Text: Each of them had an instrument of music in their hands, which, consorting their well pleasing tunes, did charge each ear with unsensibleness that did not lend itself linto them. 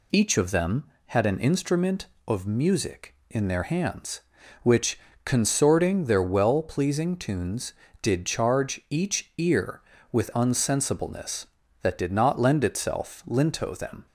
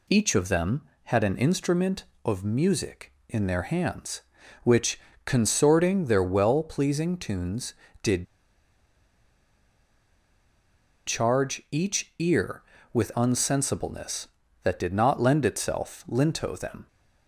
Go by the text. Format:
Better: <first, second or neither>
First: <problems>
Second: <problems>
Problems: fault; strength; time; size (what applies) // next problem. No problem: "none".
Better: first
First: none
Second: pauses between "did" and "charge"; strong; at 8.2 s; 2.8 s long